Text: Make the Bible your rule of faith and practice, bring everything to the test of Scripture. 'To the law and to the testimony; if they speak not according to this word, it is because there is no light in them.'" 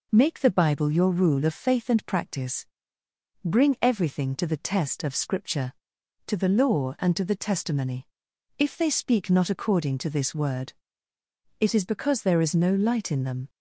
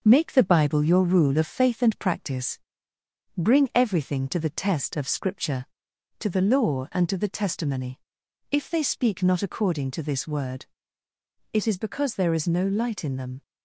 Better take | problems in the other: first | gets quieter; slight; throughout; 3 dB

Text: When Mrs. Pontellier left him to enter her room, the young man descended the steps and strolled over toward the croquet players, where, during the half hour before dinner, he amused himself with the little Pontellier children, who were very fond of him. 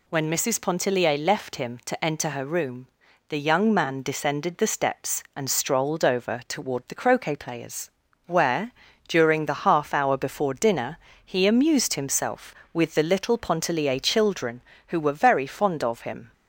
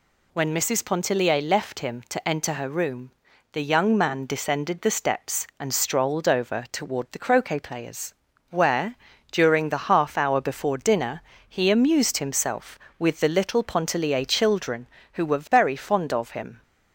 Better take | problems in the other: neither | none

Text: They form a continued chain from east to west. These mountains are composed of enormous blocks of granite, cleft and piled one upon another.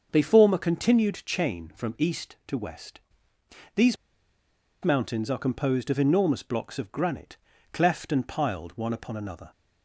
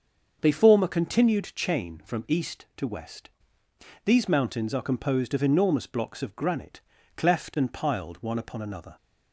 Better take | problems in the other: second | starts louder than the rest; until 1.1 s; 6.5 dB; also in the second // pauses between "These" and "mountains"; noticeable; at 3.9 s; 0.88 s long

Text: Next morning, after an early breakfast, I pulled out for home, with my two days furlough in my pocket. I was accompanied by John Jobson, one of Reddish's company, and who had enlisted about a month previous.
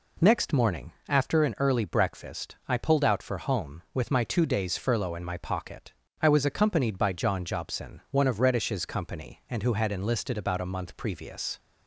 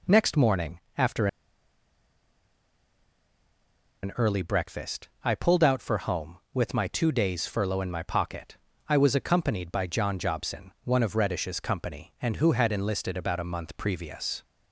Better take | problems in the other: first | pauses between "after" and "an"; strong; at 1.2 s; 2.7 s long

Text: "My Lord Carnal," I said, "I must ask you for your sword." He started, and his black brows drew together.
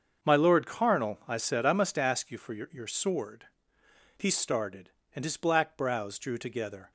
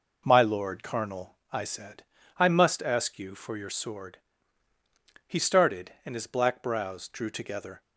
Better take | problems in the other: second | starts louder than the rest; until 1.3 s; 6.5 dB // says "your" twice; at 2.7 s

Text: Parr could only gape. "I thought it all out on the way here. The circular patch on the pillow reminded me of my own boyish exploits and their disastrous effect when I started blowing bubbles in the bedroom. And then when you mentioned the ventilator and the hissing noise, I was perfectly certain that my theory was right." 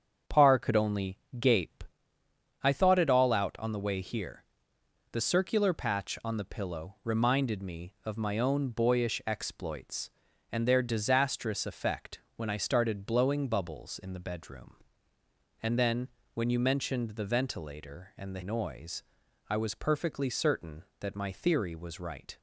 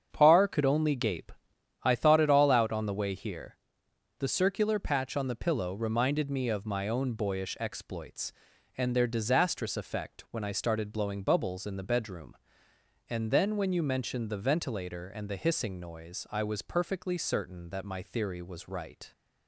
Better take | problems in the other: second | starts louder than the rest; strong; until 1.4 s; 7.5 dB; strong in the second // pauses between "only" and "gape"; slight; at 1.1 s; 0.20 s long // pauses between "effect" and "when"; slight; at 12.2 s; 0.16 s long // pauses between "then" and "when"; slight; at 16.0 s; 0.26 s long // skips "hissing"; at 18.4 s

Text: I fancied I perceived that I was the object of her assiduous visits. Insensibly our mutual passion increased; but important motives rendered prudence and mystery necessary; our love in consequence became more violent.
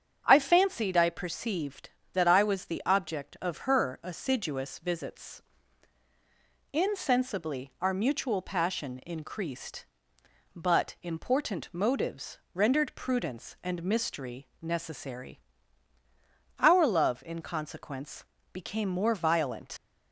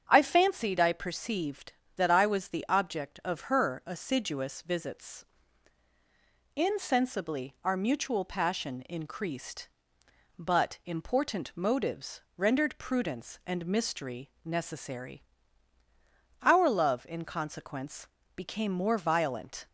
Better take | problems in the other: second | starts louder than the rest; strong; until 1.2 s; 7.5 dB; strong in the second // pauses between "motives" and "rendered"; slight; at 12.3 s; 0.16 s long; slight in the second // pauses between "consequence" and "became"; slight; at 18.2 s; 0.30 s long; slight in the second // leaves "violent" unfinished; at 19.7 s; 70 ms

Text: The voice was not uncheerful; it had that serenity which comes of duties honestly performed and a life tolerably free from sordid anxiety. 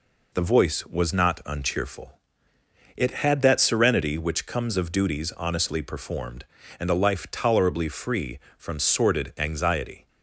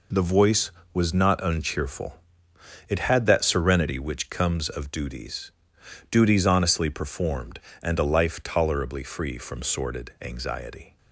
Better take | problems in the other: first | says "duties" twice; at 6.0 s

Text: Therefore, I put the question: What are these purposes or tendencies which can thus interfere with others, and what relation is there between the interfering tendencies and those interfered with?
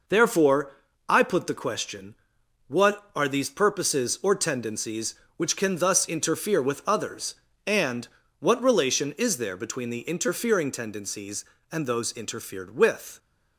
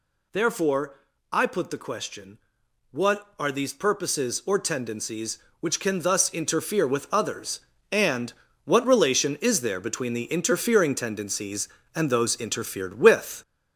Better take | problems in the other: first | gets louder; noticeable; throughout; 4.5 dB // pauses between "and" and "what"; slight; at 8.3 s; 0.34 s long; slight in the first

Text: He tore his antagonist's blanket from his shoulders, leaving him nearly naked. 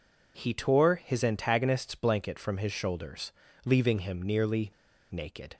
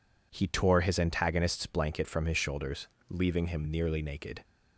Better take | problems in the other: second | pauses between "nearly" and "naked"; at 4.6 s; 0.40 s long

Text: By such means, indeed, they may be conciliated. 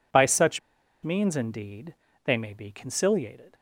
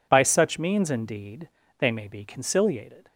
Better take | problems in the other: second | pauses between "such" and "means"; at 0.5 s; 0.43 s long

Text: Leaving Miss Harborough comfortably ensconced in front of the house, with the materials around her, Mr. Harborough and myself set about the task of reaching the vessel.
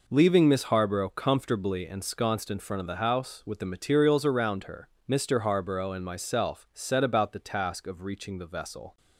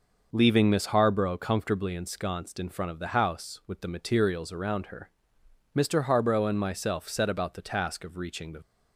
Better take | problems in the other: first | stops before "vessel"; at 8.6 s

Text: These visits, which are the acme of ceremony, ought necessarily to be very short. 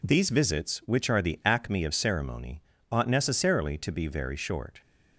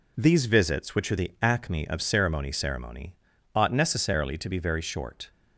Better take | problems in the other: first | says "ceremony" twice; at 2.4 s

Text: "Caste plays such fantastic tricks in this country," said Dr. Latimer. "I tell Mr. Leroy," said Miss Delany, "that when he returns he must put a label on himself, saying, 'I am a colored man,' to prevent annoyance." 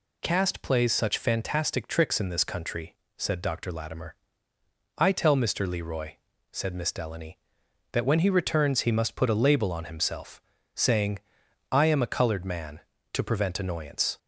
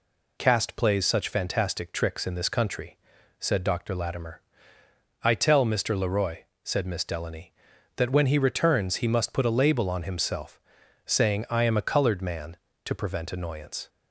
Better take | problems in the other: neither | none

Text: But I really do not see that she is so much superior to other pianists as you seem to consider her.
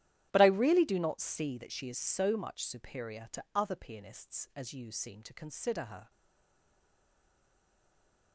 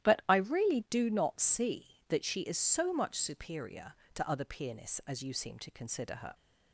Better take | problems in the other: second | starts louder than the rest; strong; until 1.3 s; 11 dB; strong in the second // stays silent after the last word; from 6.0 s on; 2.3 s long

